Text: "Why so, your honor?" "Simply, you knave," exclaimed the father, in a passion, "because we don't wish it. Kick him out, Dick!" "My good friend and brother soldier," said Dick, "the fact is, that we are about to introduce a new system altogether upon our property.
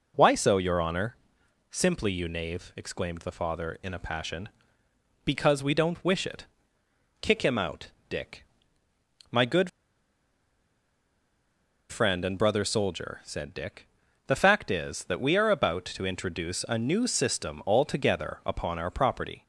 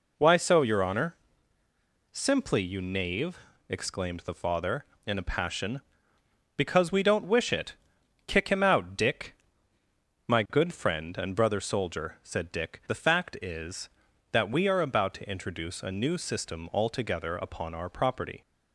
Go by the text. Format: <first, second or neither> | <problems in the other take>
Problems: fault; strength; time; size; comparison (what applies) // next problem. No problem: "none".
second | pauses between "good" and "friend"; strong; at 9.6 s; 2.2 s long